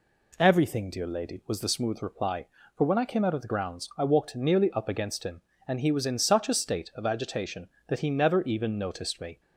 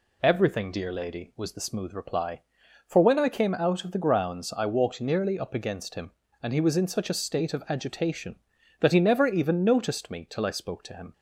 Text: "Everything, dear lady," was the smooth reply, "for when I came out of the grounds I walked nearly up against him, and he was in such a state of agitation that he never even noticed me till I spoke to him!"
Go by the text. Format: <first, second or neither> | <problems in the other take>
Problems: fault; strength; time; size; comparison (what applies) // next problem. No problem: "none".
second | stops before "till I spoke to him"; at 9.4 s